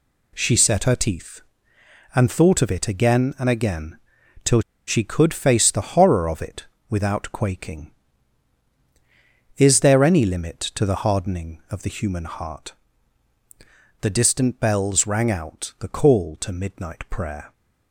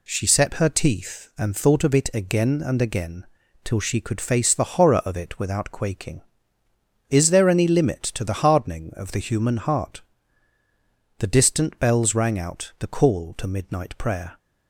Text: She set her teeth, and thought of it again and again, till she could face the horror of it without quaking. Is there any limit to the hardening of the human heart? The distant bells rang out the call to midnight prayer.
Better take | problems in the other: second | pauses between "till" and "she"; slight; at 4.6 s; 0.27 s long // pauses between "it" and "without"; slight; at 6.6 s; 0.24 s long

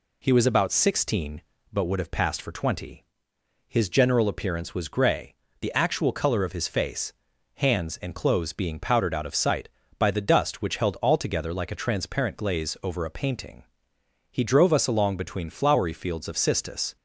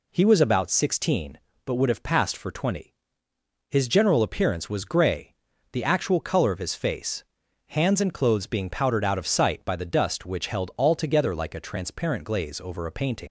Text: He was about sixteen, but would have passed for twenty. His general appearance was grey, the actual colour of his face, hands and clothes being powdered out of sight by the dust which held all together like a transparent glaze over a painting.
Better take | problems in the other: second | goes on to say "He drove us along between flowery fields of cistus"; strong; from 14.3 s on; 2.6 s long

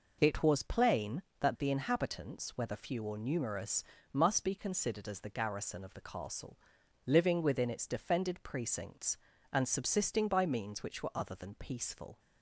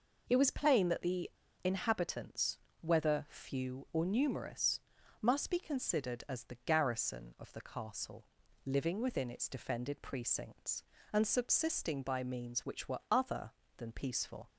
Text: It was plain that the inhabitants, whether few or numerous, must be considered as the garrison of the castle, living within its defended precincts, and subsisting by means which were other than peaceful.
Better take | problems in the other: first | pauses between "the" and "inhabitants"; slight; at 1.2 s; 0.33 s long

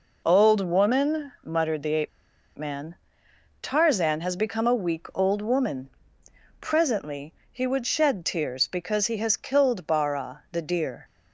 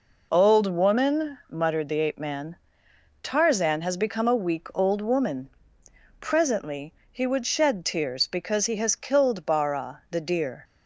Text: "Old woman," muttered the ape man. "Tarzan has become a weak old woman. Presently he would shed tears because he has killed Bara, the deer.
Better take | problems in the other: second | pauses between "ape" and "man"; noticeable; at 2.0 s; 0.47 s long // pauses between "Presently" and "he"; slight; at 7.3 s; 0.18 s long; slight in the second

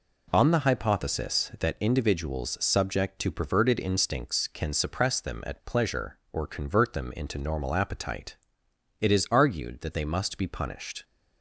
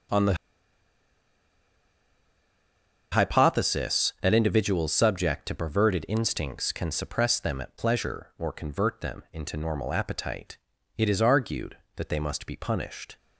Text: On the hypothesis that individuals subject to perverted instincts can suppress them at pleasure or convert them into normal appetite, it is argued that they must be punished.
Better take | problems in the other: first | starts louder than the rest; noticeable; until 3.9 s; 6 dB // pauses between "the" and "hypothesis"; strong; at 0.3 s; 2.7 s long

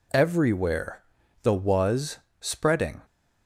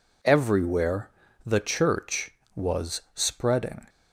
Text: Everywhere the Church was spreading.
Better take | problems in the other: second | pauses between "Everywhere" and "the"; at 1.0 s; 0.40 s long; slight in the second // skips "Church"; at 1.5 s // pauses between "was" and "spreading"; slight; at 2.1 s; 0.24 s long

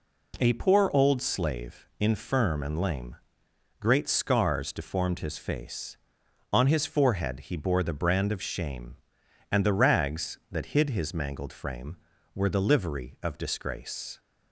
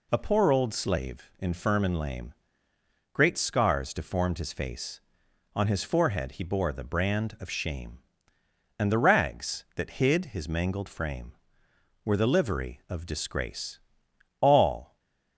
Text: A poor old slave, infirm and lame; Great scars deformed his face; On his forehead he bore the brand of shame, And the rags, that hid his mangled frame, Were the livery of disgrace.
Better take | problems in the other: first | goes on to say "All"; from 14.4 s on; 0.58 s long // stays silent after the last word; slight; from 14.8 s on; 0.5 s long

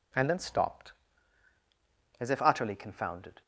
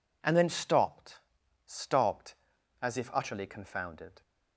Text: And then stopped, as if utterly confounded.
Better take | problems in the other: first | says "stopped" twice; at 1.7 s

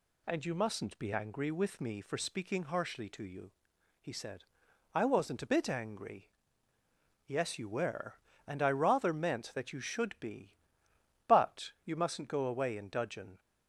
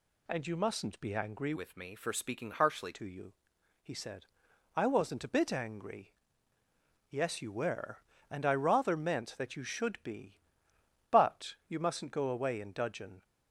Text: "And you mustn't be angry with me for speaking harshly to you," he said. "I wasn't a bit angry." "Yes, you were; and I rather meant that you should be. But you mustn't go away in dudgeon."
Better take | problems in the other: first | changes voice from "with" to "harshly"; from 1.5 to 2.9 s; 1.4 s long

